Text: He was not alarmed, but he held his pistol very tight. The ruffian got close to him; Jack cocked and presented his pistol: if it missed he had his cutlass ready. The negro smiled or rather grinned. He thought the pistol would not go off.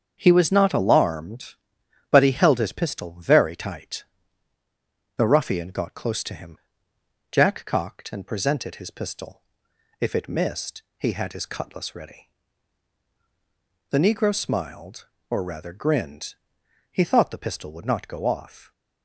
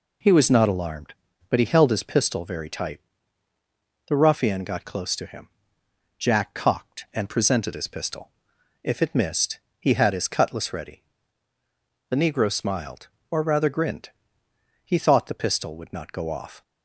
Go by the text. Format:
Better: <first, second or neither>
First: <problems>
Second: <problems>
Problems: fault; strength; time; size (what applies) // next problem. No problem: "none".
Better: second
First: starts louder than the rest; strong; until 1.4 s; 7 dB // pauses between "missed" and "he"; slight; at 10.8 s; 0.16 s long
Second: pauses between "missed" and "he"; slight; at 9.5 s; 0.22 s long